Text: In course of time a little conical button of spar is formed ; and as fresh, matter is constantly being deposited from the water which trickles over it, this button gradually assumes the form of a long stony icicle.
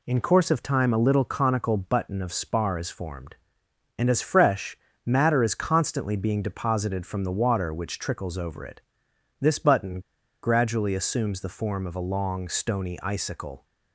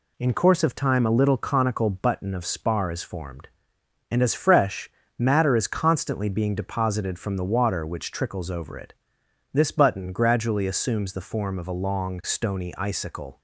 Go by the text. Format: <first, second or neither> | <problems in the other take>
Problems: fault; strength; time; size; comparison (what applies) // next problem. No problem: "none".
second | pauses between "button" and "gradually"; at 9.9 s; 0.43 s long